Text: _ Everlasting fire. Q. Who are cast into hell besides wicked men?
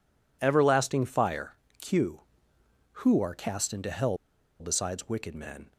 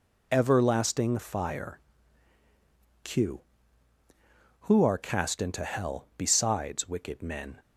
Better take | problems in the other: second | pauses between "hell" and "besides"; at 4.1 s; 0.43 s long

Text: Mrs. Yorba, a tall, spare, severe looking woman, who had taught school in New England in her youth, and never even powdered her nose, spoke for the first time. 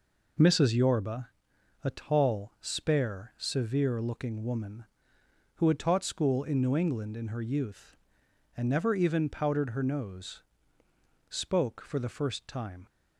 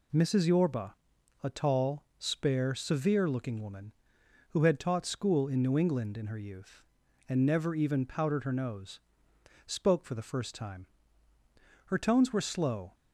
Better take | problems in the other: first | goes on to say "Her tones were slow"; noticeable; from 11.8 s on; 1.0 s long

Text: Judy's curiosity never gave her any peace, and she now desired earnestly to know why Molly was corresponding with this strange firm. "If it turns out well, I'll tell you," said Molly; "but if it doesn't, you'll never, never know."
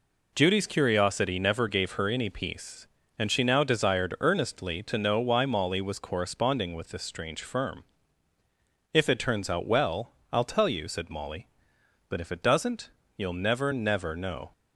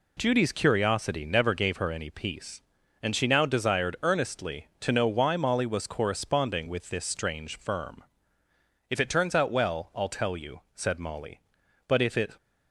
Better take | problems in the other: first | stops before "doesn't you'll never never know"; at 12.3 s

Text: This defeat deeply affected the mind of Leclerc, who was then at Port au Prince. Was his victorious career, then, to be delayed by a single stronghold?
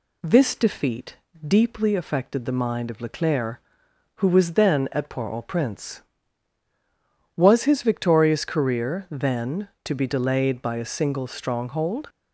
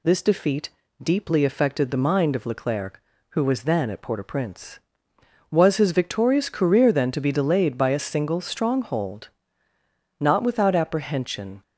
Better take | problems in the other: first | pauses between "defeat" and "deeply"; slight; at 0.6 s; 0.34 s long; slight in the first // goes on to say "Not without apprehension"; from 10.2 s on; 1.4 s long

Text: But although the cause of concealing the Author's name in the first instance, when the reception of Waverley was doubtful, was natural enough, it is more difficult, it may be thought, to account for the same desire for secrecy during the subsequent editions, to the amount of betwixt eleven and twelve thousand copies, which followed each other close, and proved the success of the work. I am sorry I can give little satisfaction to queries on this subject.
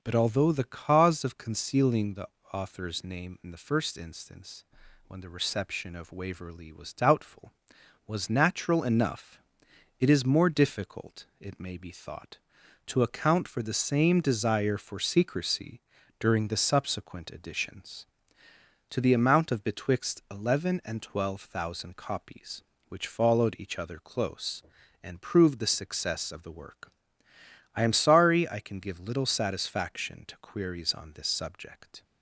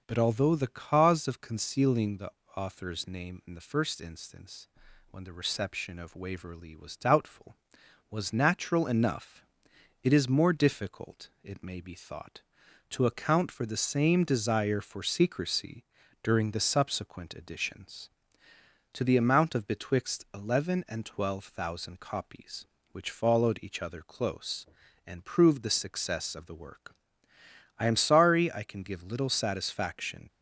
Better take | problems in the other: first | pauses between "the" and "Author's"; slight; at 2.2 s; 0.26 s long; slight in the first // pauses between "secrecy" and "during"; at 15.8 s; 0.38 s long; also in the first // stops before "to queries on this subject"; at 30.2 s

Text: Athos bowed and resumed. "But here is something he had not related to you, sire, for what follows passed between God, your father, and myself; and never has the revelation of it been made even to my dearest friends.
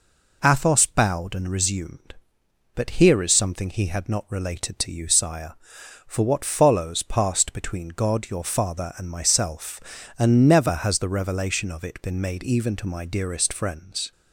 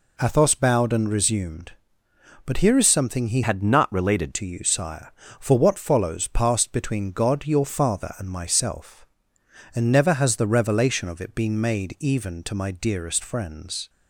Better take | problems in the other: first | changes voice from "had" to "related"; from 3.4 to 4.3 s; 0.9 s long

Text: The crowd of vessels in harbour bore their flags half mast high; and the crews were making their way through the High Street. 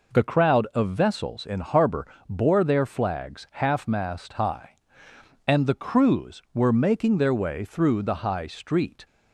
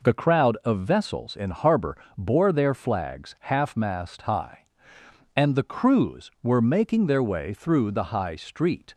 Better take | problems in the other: neither | pauses between "harbour" and "bore"; slight; the same in both

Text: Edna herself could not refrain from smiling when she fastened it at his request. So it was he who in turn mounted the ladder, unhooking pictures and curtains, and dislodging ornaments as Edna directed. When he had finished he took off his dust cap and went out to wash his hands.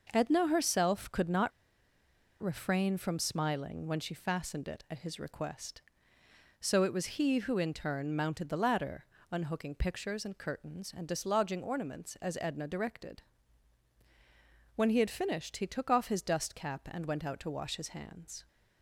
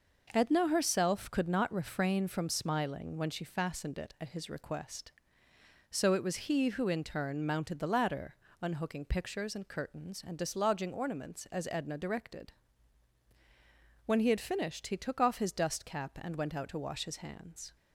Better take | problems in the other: second | pauses between "not" and "refrain"; noticeable; at 1.5 s; 0.89 s long

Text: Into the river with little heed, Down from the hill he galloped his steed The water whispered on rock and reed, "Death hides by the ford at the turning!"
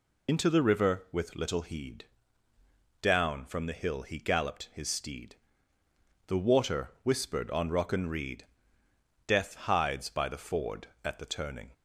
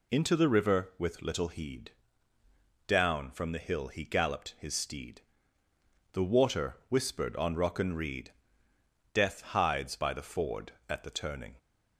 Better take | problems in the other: second | loses the start of "Into"; at 0.2 s; 40 ms // pauses between "steed" and "The"; noticeable; at 5.3 s; 0.92 s long; noticeable in the second

